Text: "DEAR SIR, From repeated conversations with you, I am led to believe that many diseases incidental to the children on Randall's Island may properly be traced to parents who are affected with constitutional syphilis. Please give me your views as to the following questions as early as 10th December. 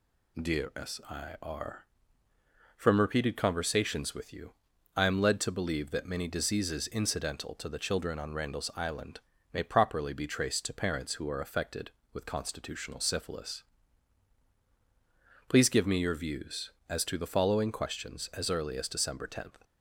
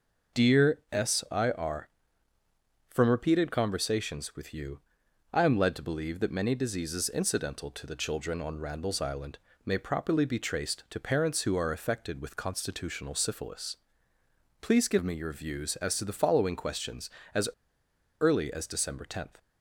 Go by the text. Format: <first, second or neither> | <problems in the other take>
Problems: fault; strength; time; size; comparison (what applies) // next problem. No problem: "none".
first | pauses between "Island" and "may"; slight; at 9.3 s; 0.26 s long; slight in the first // pauses between "as" and "early"; noticeable; at 17.4 s; 0.72 s long